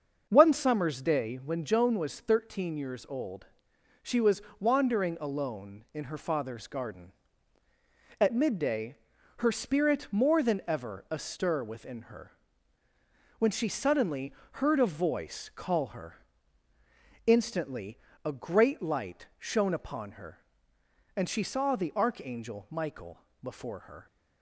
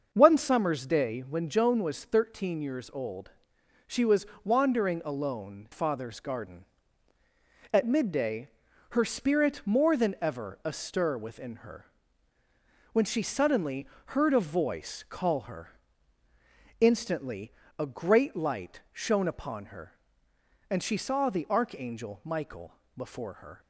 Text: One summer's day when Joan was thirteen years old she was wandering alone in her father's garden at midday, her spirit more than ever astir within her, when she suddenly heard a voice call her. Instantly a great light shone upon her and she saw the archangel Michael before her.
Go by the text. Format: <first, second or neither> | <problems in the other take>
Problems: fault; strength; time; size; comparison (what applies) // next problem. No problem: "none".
first | starts louder than the rest; until 1.1 s; 6 dB; also in the first // pauses between "old" and "she"; noticeable; at 3.2 s; 0.56 s long; noticeable in the first // pauses between "was" and "wandering"; slight; at 4.2 s; 0.18 s long; slight in the first // skips "in her"; at 5.6 s // pauses between "suddenly" and "heard"; slight; at 13.8 s; 0.20 s long; slight in the first // pauses between "Instantly" and "a"; slight; at 17.5 s; 0.26 s long; slight in the first // pauses between "Michael" and "before"; slight; at 22.7 s; 0.24 s long; slight in the first